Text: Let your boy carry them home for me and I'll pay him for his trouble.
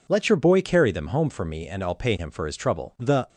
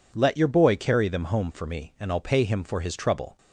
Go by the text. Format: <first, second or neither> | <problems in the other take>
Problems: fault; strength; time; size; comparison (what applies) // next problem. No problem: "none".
second | goes on to say "The"; slight; from 2.9 s on; 0.30 s long